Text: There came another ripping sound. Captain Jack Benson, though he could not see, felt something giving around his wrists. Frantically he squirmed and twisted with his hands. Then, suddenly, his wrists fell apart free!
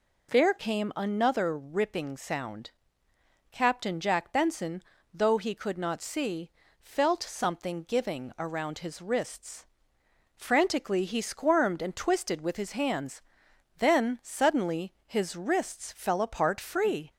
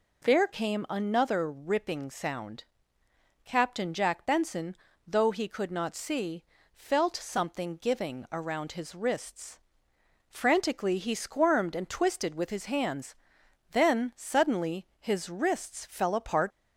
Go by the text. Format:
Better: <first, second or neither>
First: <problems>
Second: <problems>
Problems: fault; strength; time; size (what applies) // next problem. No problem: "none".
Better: first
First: none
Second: stops before "free"; at 16.5 s